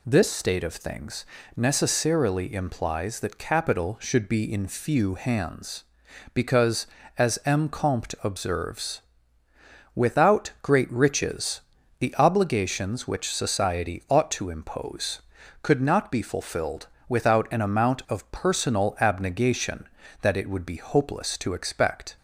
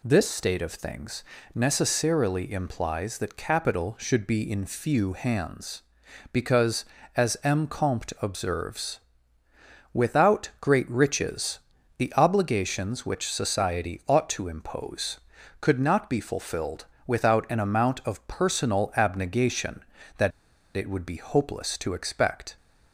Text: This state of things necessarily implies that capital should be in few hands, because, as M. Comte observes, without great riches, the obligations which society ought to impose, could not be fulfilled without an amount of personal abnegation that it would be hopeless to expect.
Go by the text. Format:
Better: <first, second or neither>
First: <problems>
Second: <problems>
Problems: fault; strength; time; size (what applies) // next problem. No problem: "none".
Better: first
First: pauses between "things" and "necessarily"; slight; at 1.2 s; 0.30 s long // pauses between "fulfilled" and "without"; slight; at 16.8 s; 0.22 s long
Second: pauses between "things" and "necessarily"; slight; at 1.2 s; 0.30 s long // pauses between "fulfilled" and "without"; slight; at 16.8 s; 0.22 s long // pauses between "that" and "it"; at 20.3 s; 0.45 s long